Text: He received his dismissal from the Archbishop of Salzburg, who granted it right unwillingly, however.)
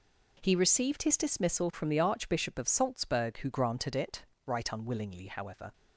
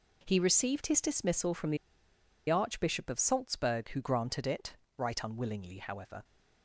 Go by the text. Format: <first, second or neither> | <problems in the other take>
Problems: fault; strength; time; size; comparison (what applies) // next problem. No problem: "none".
first | pauses between "the" and "Archbishop"; noticeable; at 1.7 s; 0.72 s long // pauses between "it" and "right"; slight; at 4.7 s; 0.22 s long; slight in the first